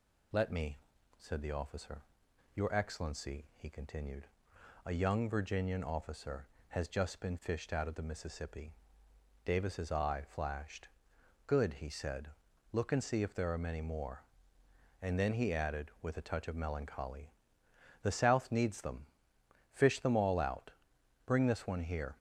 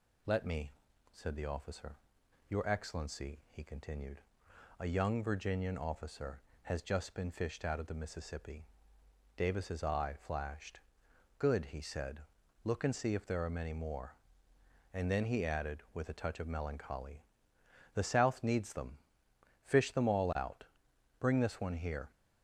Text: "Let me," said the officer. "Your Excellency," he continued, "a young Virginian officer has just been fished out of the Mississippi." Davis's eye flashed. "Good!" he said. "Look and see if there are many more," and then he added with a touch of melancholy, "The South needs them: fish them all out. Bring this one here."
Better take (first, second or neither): neither